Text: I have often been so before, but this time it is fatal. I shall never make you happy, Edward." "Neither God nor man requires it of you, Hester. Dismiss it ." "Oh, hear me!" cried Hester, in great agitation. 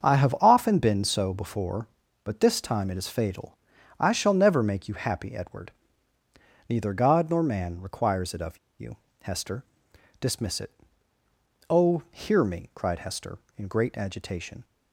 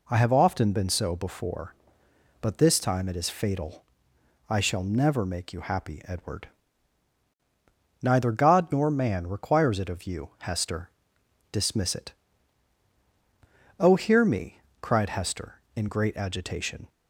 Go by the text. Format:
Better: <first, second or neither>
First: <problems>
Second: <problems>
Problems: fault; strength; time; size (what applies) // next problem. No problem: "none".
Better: second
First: starts louder than the rest; strong; until 1.1 s; 7 dB // pauses between "of" and "you"; slight; at 8.5 s; 0.21 s long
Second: none